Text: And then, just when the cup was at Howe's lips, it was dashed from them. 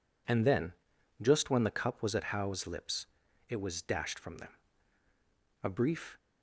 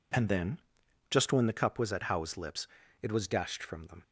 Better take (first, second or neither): second